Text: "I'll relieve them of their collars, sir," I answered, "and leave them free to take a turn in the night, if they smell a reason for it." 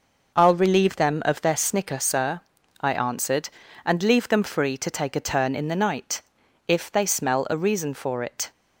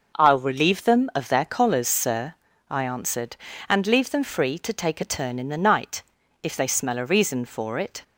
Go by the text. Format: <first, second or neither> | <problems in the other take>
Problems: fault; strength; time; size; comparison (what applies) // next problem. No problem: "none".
second | says "snicker" for "collars"; at 1.5 s